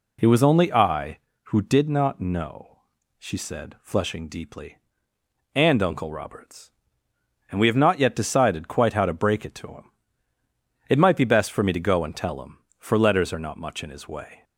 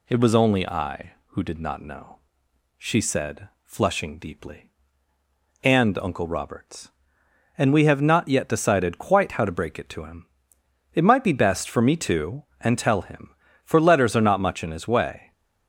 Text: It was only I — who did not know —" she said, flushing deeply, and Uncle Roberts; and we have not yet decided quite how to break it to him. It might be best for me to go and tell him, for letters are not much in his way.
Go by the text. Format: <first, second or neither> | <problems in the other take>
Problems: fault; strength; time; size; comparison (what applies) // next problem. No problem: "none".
first | skips "go"; at 12.5 s